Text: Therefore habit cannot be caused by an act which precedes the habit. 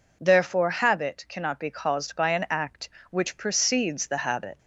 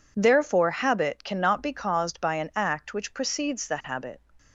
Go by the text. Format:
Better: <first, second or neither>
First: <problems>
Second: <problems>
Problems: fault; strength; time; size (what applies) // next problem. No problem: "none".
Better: neither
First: none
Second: none